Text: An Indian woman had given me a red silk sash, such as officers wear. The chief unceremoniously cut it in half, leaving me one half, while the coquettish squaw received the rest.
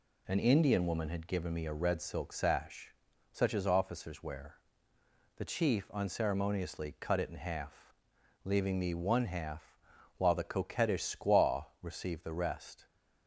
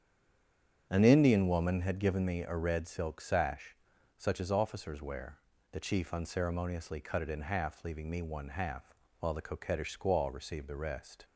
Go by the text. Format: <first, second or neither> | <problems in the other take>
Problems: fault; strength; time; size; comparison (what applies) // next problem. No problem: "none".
first | stays silent before the first word; slight; until 0.9 s; 0.9 s long // starts louder than the rest; strong; until 1.9 s; 8.5 dB